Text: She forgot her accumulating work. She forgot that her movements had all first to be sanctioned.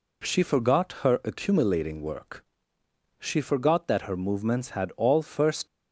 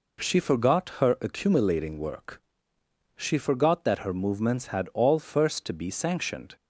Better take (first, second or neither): second